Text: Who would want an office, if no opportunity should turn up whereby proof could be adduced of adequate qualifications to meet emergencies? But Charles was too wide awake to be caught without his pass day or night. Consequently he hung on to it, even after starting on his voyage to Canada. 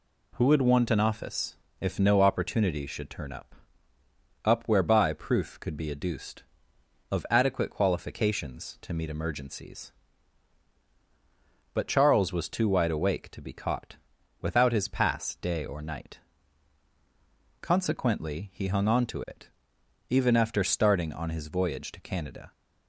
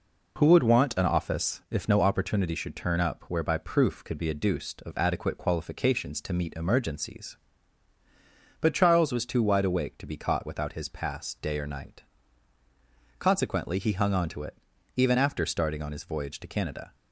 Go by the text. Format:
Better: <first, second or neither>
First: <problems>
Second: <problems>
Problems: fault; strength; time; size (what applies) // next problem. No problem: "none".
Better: second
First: says "up" twice; at 4.4 s // pauses between "caught" and "without"; noticeable; at 13.9 s; 0.46 s long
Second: none